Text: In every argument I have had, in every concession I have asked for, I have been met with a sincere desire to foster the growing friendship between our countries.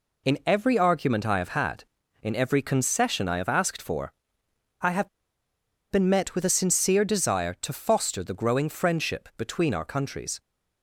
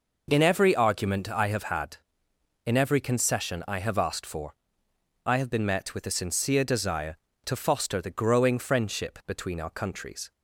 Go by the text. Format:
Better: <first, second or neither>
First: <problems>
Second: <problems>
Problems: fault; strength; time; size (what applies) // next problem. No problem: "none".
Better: second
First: pauses between "have" and "been"; noticeable; at 5.0 s; 0.82 s long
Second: none